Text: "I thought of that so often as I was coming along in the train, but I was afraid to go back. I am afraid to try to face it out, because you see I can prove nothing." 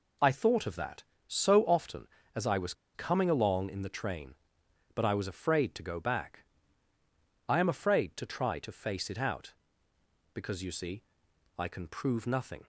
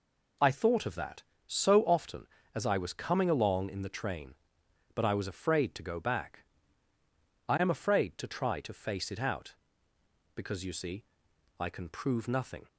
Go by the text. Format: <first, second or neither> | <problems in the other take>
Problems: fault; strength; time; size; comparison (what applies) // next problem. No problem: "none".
second | pauses between "was" and "coming"; slight; at 2.7 s; 0.22 s long // pauses between "see" and "I"; noticeable; at 11.0 s; 0.54 s long; noticeable in the second